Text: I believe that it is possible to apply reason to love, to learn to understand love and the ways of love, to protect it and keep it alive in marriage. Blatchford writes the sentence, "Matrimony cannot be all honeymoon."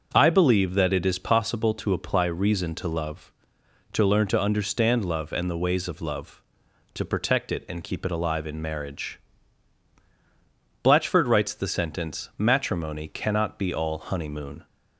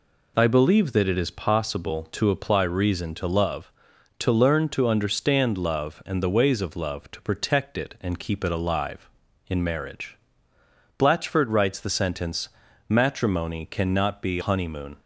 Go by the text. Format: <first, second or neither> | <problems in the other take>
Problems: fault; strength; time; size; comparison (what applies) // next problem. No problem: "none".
first | skips "all"; at 14.4 s